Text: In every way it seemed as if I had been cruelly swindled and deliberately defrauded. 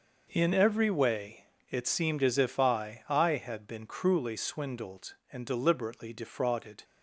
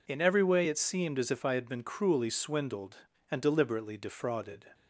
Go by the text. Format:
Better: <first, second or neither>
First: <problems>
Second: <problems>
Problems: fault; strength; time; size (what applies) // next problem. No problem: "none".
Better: second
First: pauses between "way" and "it"; slight; at 1.4 s; 0.24 s long // says "I" twice; at 3.0 s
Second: none